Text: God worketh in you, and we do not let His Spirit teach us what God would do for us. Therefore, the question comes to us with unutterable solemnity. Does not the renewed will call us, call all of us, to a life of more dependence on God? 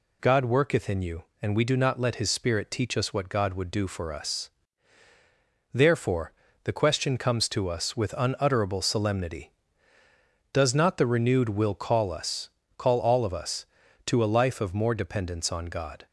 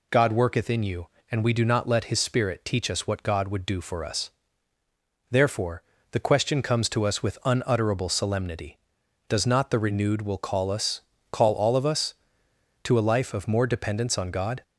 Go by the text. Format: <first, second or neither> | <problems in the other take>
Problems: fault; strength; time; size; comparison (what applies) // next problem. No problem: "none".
neither | none